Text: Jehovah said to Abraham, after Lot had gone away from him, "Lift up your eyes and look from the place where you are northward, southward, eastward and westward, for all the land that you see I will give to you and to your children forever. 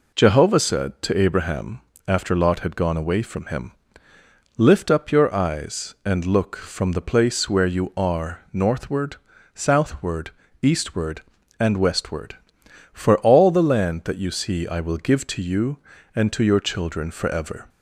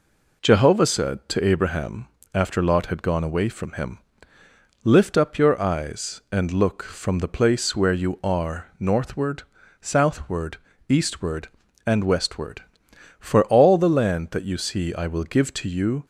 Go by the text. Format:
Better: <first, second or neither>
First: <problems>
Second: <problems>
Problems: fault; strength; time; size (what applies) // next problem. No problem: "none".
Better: first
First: none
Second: stops before "and to your children forever"; at 16.0 s